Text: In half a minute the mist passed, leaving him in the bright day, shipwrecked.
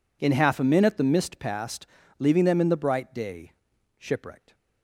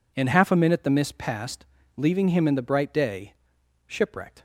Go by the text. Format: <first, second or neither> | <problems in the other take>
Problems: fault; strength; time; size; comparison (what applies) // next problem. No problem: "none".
second | says "them" for "him"; at 2.4 s